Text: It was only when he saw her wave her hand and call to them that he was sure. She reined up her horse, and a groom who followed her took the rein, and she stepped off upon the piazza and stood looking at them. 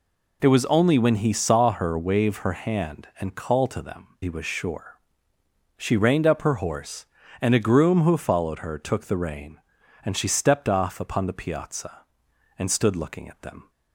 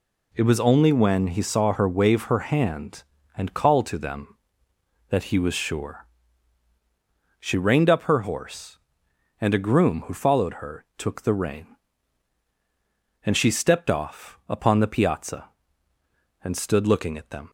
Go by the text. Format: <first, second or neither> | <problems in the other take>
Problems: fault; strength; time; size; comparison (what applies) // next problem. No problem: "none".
second | skips "that"; at 4.1 s